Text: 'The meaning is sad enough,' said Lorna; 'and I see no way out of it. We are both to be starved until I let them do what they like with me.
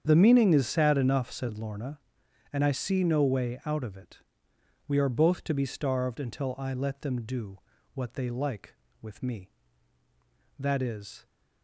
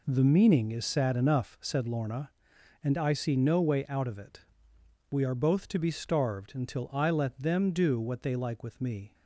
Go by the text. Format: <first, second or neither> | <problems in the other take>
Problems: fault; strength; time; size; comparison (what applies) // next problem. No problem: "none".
second | starts louder than the rest; strong; until 1.0 s; 8 dB // pauses between "do" and "what"; slight; at 7.5 s; 0.36 s long // goes on to say "That is"; noticeable; from 10.5 s on; 0.66 s long